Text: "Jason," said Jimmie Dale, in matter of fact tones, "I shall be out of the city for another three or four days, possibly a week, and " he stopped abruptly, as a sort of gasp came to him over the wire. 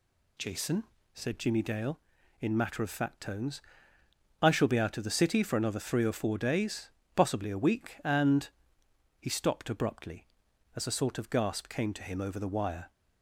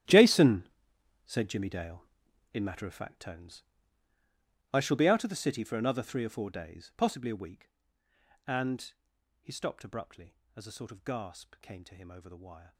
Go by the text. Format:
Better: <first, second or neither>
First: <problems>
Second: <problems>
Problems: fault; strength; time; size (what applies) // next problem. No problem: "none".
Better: first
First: none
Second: gets quieter; strong; throughout; 19 dB